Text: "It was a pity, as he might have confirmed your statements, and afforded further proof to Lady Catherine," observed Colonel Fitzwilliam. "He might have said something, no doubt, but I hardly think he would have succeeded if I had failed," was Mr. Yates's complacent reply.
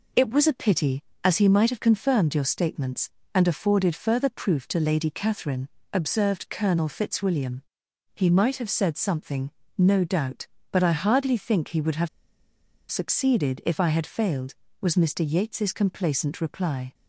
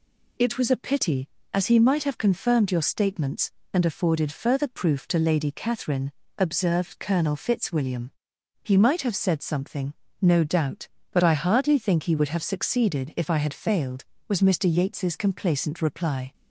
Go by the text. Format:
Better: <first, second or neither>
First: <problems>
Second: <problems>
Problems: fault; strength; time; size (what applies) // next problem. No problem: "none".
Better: second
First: pauses between "have" and "succeeded"; noticeable; at 12.0 s; 0.83 s long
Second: none